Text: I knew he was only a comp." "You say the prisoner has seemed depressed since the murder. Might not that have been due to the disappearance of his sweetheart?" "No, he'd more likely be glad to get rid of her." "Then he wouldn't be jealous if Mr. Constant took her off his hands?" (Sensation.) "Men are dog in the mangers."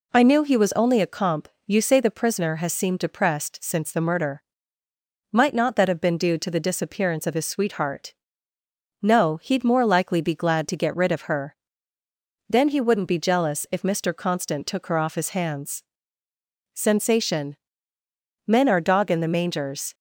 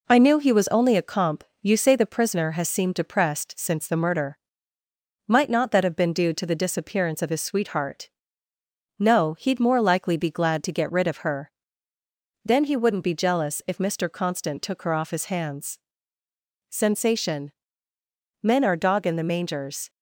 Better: first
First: none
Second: gets quieter; slight; throughout; 3 dB

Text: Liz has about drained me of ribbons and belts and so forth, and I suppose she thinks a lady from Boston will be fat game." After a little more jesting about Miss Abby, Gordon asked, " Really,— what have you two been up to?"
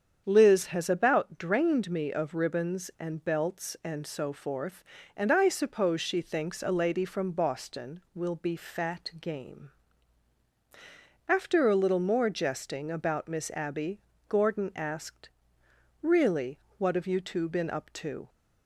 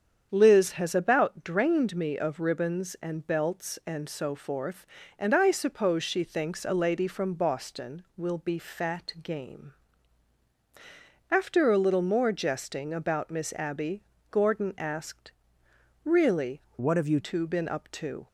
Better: first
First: starts louder than the rest; strong; until 1.2 s; 7.5 dB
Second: starts louder than the rest; strong; until 1.3 s; 7.5 dB // changes voice from "what" to "you"; from 16.7 to 17.1 s; 0.4 s long

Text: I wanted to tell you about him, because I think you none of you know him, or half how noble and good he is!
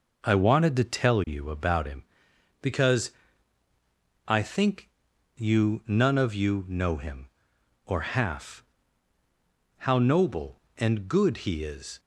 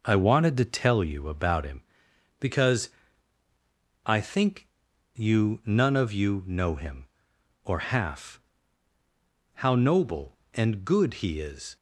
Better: neither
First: pauses between "because" and "I"; at 3.1 s; 1.1 s long // pauses between "think" and "you"; noticeable; at 4.8 s; 0.48 s long // pauses between "half" and "how"; at 8.6 s; 1.1 s long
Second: pauses between "because" and "I"; at 2.8 s; 1.1 s long // pauses between "think" and "you"; noticeable; at 4.6 s; 0.48 s long // pauses between "half" and "how"; at 8.3 s; 1.1 s long

